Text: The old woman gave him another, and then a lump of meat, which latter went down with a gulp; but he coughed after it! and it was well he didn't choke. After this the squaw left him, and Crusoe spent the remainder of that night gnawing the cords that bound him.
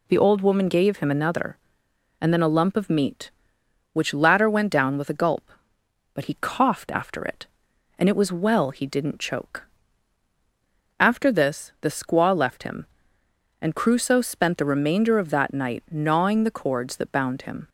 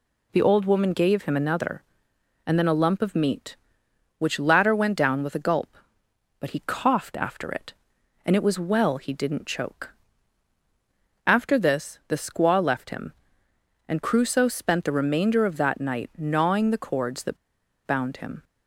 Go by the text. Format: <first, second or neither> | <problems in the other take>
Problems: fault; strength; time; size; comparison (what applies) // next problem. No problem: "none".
first | pauses between "that" and "bound"; noticeable; at 17.3 s; 0.50 s long